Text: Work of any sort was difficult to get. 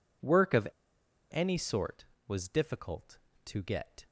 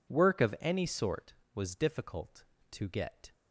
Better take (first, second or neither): second